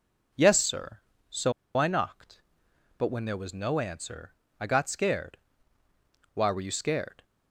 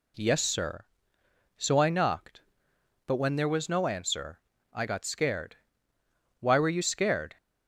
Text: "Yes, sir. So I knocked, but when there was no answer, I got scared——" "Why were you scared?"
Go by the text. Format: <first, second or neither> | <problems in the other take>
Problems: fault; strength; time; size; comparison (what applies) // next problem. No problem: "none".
second | pauses between "So" and "I"; slight; at 1.5 s; 0.24 s long